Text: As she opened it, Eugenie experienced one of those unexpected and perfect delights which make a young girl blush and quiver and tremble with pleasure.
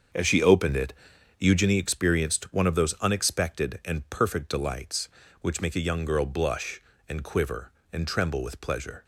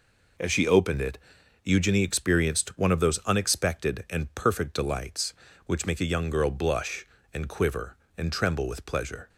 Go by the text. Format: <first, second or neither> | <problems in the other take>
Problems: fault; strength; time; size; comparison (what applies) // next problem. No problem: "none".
second | starts louder than the rest; until 1.8 s; 7 dB